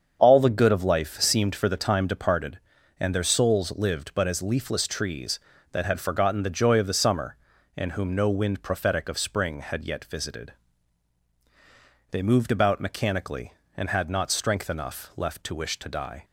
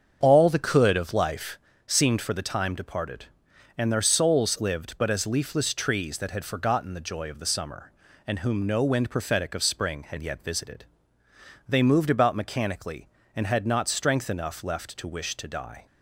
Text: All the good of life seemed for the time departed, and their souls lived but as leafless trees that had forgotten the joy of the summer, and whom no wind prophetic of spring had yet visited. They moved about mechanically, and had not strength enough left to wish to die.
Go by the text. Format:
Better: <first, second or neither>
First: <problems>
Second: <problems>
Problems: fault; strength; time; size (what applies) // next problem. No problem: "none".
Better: first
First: starts louder than the rest; strong; until 1.2 s; 7.5 dB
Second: starts louder than the rest; strong; until 1.2 s; 7 dB // says "could" for "good"; at 0.5 s // pauses between "life" and "seemed"; slight; at 1.5 s; 0.30 s long